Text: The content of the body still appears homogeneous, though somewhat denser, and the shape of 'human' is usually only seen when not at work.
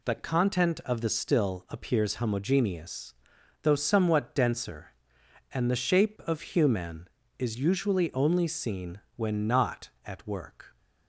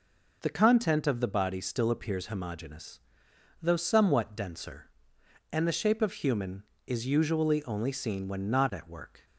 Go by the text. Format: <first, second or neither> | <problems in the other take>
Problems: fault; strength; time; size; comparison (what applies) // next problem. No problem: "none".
second | skips "body"; at 1.0 s // pauses between "seen" and "when"; slight; at 9.0 s; 0.16 s long